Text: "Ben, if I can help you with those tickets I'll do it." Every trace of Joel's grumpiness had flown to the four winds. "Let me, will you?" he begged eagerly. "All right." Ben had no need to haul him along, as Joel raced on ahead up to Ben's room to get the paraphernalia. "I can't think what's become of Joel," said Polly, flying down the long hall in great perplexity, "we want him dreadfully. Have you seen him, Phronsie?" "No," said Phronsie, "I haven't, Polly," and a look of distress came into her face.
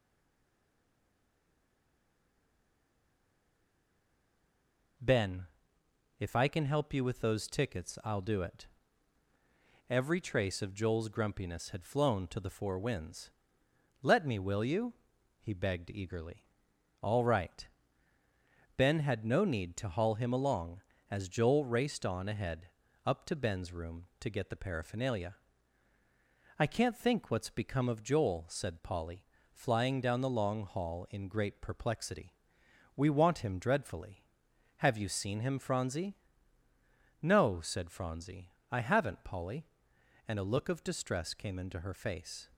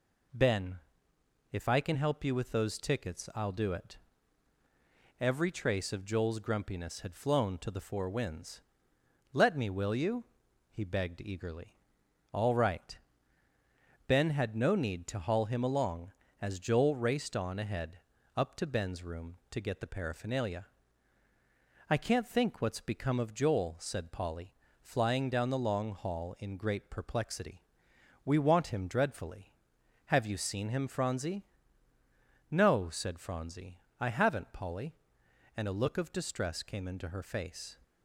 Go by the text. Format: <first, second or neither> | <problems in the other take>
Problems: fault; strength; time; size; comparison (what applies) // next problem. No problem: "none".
second | stays silent before the first word; strong; until 4.9 s; 4.9 s long // pauses between "ahead" and "up"; slight; at 22.6 s; 0.36 s long; slight in the second